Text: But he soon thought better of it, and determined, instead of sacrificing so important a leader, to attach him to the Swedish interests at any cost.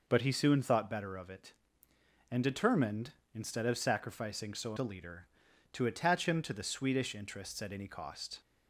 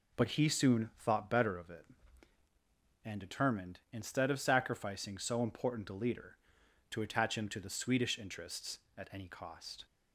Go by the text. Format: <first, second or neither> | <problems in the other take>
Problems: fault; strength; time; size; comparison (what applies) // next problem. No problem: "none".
second | skips "important"; at 4.7 s